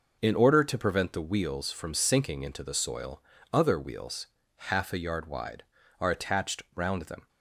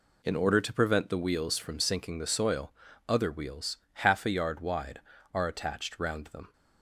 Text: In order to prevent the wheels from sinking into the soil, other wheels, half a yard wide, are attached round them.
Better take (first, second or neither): first